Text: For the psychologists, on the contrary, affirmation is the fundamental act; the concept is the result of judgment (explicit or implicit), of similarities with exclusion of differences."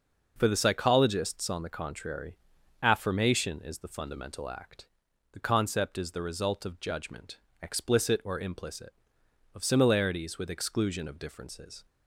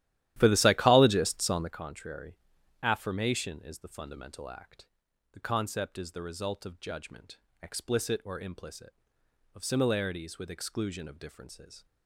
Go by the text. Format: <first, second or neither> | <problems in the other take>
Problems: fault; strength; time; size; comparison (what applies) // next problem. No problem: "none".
first | starts louder than the rest; strong; until 1.8 s; 13 dB